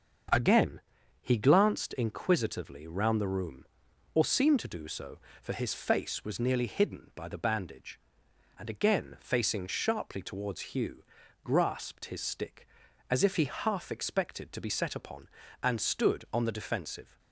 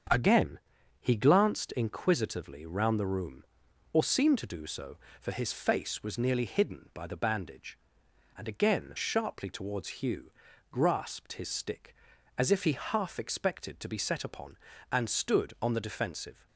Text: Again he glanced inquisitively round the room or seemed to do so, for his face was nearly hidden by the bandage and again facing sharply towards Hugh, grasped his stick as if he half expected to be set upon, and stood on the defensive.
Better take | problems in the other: first | starts louder than the rest; strong; until 1.5 s; 7.5 dB; also in the first // pauses between "Again" and "he"; at 0.5 s; 0.42 s long; also in the first // skips "facing"; at 8.9 s

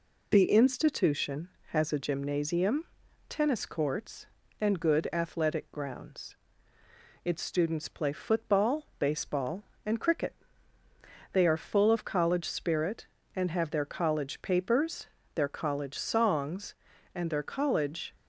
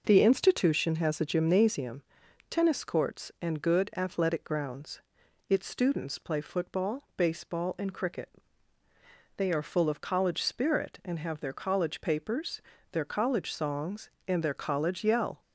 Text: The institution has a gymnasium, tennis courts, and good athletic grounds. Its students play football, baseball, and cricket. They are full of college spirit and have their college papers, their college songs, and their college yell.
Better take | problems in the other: second | stops before "yell"; at 18.1 s

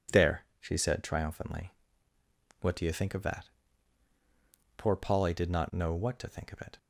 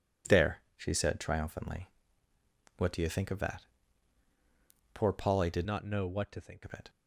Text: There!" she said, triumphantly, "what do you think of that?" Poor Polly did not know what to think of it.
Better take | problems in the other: first | changes voice from "not" to "think"; from 5.6 to 6.6 s; 1.0 s long

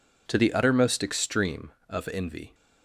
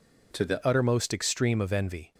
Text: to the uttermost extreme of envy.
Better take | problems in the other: first | changes voice at "uttermost"; from 0.6 s on; 1.5 s long

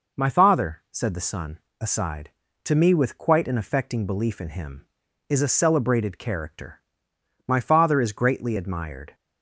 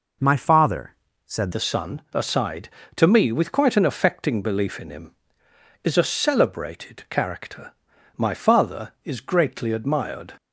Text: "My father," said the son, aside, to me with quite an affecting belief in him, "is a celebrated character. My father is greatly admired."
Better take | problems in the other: first | changes voice at "the"; from 1.5 s on; 8.8 s long

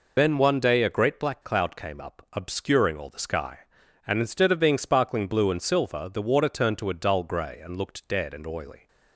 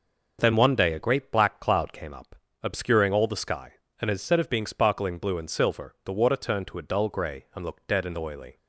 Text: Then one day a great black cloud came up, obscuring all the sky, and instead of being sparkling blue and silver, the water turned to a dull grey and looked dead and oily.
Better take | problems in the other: second | loses the start of "Then"; at 0.1 s; 55 ms

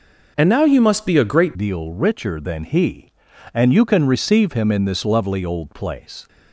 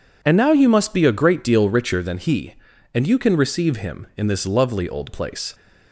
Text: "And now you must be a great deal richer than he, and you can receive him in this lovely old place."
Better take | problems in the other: second | changes voice at "deal"; from 1.5 s on; 4.7 s long

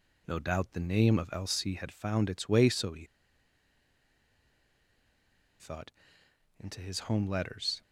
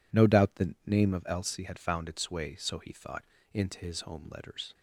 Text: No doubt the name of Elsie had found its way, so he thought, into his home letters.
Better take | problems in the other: second | pauses between "he" and "thought"; strong; at 3.0 s; 2.5 s long

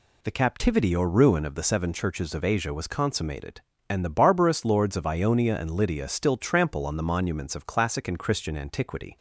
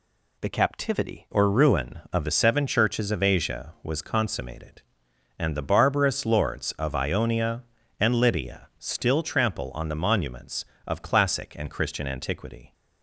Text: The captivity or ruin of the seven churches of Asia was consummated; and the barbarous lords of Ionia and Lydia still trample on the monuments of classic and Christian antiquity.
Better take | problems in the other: first | changes voice at "or"; from 1.3 s on; 11.4 s long

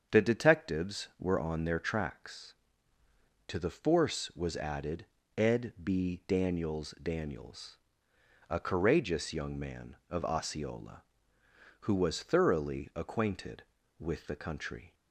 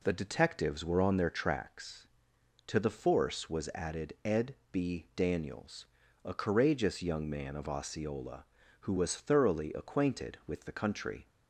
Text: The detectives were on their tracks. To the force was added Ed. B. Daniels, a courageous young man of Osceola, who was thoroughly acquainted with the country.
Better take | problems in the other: second | starts louder than the rest; strong; until 1.2 s; 7 dB // pauses between "added" and "Ed"; slight; at 5.0 s; 0.32 s long // says "Daniels" twice; at 7.0 s

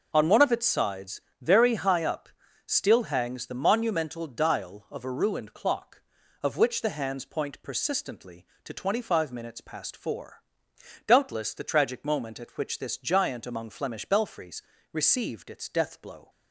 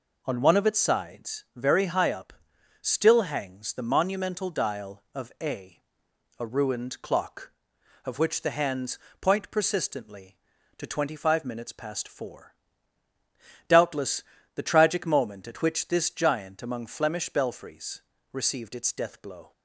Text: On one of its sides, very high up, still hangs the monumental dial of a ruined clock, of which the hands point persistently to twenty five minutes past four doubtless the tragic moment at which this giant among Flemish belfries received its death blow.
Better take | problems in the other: first | says "a" twice; at 6.3 s // pauses between "hands" and "point"; slight; at 8.9 s; 0.22 s long // pauses between "four" and "doubtless"; at 12.5 s; 1.1 s long; noticeable in the first // pauses between "doubtless" and "the"; slight; at 14.2 s; 0.34 s long // pauses between "belfries" and "received"; slight; at 18.0 s; 0.32 s long; slight in the first

